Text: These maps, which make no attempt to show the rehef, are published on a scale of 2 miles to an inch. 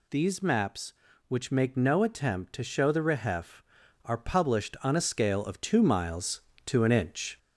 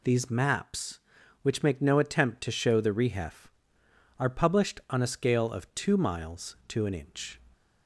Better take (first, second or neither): second